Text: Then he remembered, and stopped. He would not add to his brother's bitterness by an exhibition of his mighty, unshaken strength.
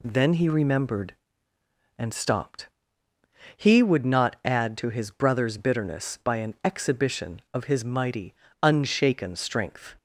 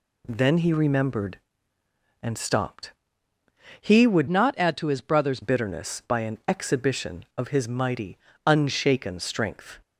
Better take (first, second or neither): first